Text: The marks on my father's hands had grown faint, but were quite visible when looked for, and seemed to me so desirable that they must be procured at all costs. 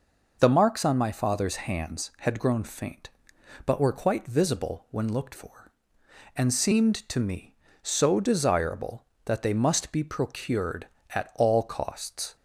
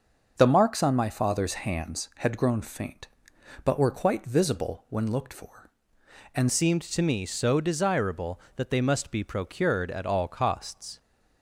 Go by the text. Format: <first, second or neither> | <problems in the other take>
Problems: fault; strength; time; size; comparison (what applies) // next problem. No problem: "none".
first | starts louder than the rest; noticeable; until 1.3 s; 6 dB // changes voice at "seemed"; from 6.5 s on; 4.4 s long